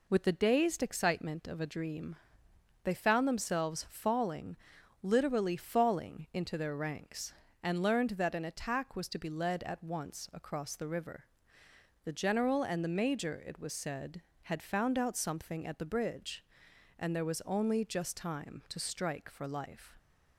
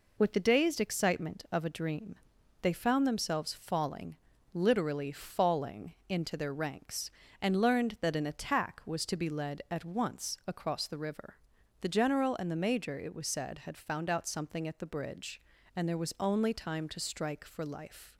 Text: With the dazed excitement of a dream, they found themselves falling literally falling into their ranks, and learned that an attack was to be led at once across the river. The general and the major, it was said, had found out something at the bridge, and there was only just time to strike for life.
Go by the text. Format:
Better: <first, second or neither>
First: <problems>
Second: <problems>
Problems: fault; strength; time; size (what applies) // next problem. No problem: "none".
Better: first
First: pauses between "falling" and "literally"; noticeable; at 4.5 s; 0.48 s long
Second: pauses between "falling" and "literally"; at 4.1 s; 0.38 s long // pauses between "falling" and "into"; slight; at 5.9 s; 0.16 s long // skips "just"; at 16.5 s